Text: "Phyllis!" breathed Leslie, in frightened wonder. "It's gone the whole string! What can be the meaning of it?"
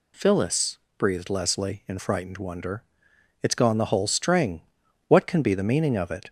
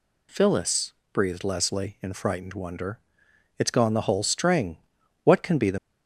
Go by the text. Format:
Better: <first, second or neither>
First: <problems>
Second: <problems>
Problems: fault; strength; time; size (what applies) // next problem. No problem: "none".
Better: first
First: none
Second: stops before "meaning of it"; at 5.7 s